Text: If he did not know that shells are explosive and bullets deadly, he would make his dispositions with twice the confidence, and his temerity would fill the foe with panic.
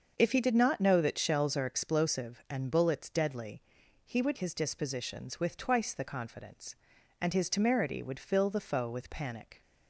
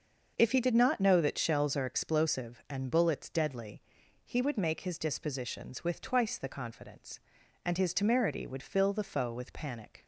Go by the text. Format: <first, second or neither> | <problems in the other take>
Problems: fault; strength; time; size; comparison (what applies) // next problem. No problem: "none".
second | starts louder than the rest; until 1.1 s; 6.5 dB; also in the second // skips "make"; at 4.3 s